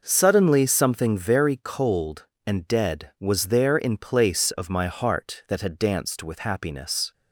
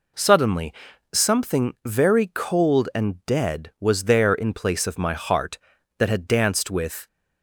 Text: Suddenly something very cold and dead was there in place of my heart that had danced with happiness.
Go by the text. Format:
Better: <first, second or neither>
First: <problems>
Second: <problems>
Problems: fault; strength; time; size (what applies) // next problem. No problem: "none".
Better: first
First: none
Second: pauses between "Suddenly" and "something"; at 0.7 s; 0.40 s long // stops before "happiness"; at 7.0 s